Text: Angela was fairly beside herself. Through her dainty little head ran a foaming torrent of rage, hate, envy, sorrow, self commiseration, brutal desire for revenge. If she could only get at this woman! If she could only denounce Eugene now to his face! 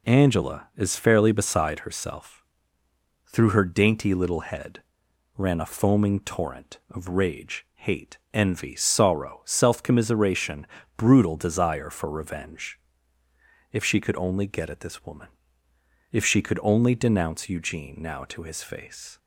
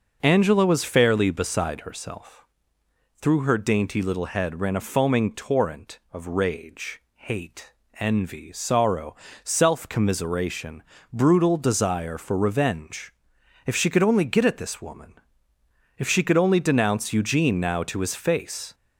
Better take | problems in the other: second | says "is" for "was"; at 0.7 s // pauses between "head" and "ran"; noticeable; at 4.7 s; 0.58 s long

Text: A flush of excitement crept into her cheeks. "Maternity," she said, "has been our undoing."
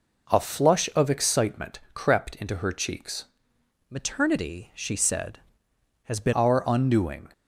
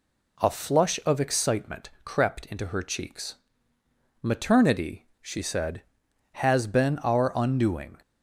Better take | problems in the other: second | pauses between "excitement" and "crept"; slight; at 1.7 s; 0.16 s long; slight in the second // changes voice from "Maternity" to "been"; from 3.8 to 6.3 s; 2.5 s long

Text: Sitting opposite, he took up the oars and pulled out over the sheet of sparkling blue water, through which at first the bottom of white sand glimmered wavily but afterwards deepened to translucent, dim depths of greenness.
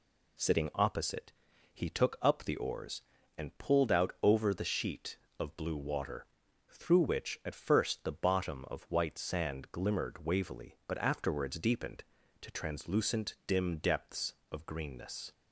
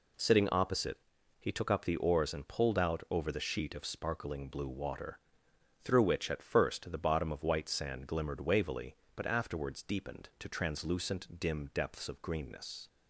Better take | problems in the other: second | skips "sparkling"; at 5.5 s

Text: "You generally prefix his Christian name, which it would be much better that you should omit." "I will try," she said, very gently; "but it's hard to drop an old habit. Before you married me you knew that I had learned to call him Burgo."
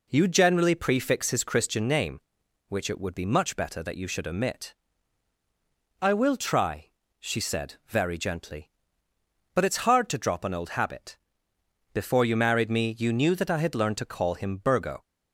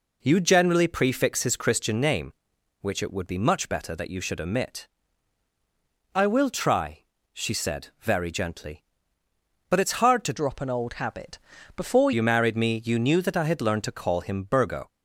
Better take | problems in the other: first | changes voice from "drop" to "Before"; from 10.3 to 12.1 s; 1.8 s long

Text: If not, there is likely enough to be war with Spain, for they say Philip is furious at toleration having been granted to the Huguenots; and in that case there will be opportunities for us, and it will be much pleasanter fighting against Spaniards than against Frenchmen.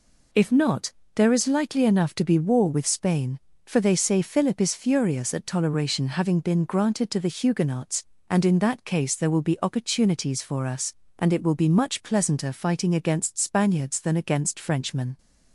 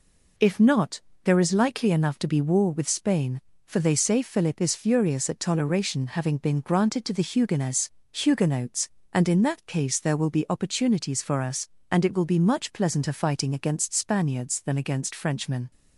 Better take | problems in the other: first | says "Huguenots" twice; at 8.1 s

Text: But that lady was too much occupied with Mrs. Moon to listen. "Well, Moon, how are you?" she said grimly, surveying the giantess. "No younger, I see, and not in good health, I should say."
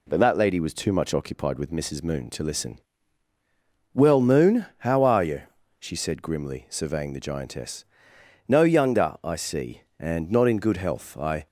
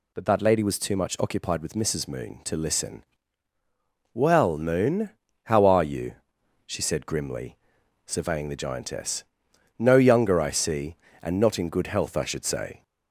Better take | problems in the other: second | stops before "should say"; at 11.4 s

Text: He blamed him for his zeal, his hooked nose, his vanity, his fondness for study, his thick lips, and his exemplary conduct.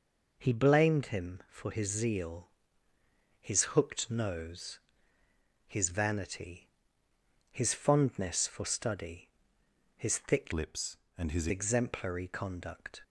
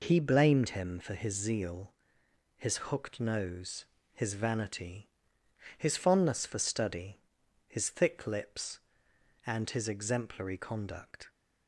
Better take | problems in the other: second | changes voice from "lips" to "his"; from 10.5 to 11.4 s; 0.9 s long

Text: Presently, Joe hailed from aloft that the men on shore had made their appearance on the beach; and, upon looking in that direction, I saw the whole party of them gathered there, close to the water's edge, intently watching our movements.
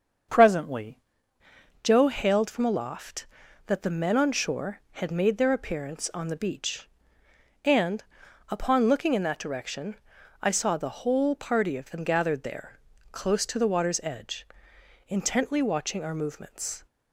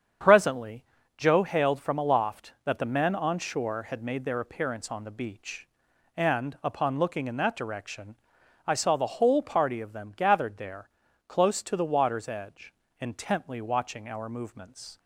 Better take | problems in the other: second | starts louder than the rest; until 2.1 s; 7 dB; strong in the second // changes voice at "Joe"; from 1.8 s on; 15.0 s long

